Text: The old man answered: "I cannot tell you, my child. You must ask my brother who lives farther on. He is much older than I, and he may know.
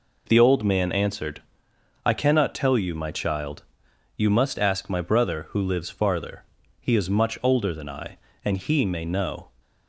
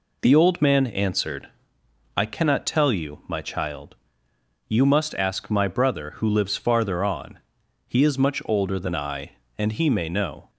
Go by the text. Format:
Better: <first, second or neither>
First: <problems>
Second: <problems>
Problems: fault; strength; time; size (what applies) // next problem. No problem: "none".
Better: second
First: skips "on"; at 6.6 s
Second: none